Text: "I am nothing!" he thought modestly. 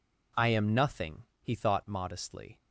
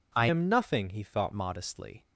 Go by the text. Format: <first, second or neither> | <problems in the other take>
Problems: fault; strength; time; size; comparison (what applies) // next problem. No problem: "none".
first | changes voice from "am" to "thought"; from 0.2 to 1.3 s; 1.1 s long